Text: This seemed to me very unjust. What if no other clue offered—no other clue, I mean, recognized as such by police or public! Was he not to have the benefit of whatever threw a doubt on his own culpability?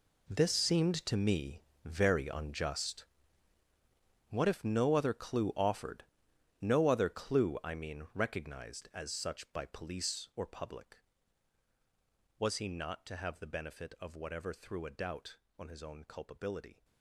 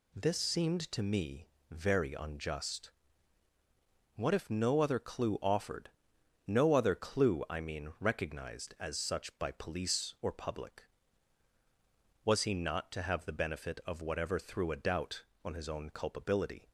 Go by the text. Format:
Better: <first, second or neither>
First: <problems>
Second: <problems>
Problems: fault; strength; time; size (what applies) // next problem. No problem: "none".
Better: second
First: gets quieter; strong; throughout; 15 dB // pauses between "me" and "very"; slight; at 1.6 s; 0.24 s long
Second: pauses between "me" and "very"; slight; at 1.4 s; 0.24 s long